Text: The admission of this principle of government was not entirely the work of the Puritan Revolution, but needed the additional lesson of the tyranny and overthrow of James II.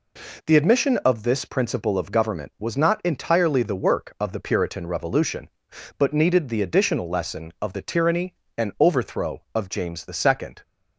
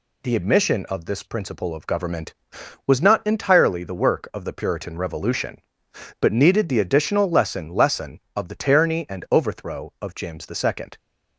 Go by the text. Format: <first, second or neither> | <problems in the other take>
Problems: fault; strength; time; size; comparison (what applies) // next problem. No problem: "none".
first | says "lesson" twice; at 7.6 s